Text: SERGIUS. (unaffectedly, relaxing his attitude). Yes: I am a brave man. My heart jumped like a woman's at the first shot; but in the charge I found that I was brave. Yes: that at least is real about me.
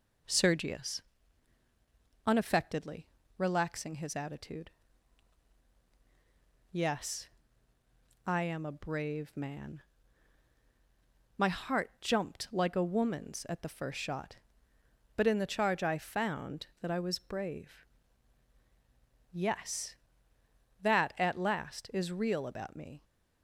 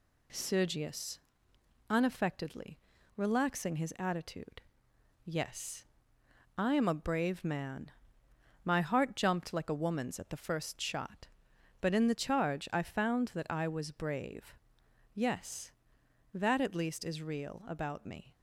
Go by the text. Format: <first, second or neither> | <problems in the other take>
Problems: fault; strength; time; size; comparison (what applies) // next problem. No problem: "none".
second | says "last" for "least"; at 21.3 s